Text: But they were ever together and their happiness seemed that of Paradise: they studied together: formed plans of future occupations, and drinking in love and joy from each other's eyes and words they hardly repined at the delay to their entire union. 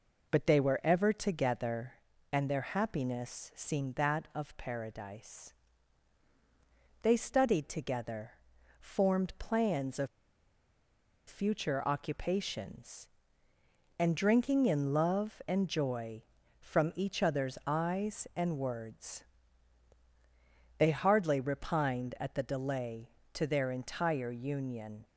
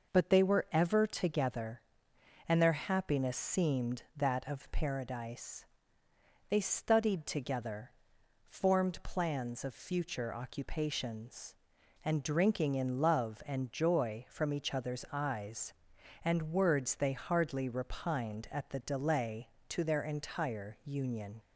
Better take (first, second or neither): second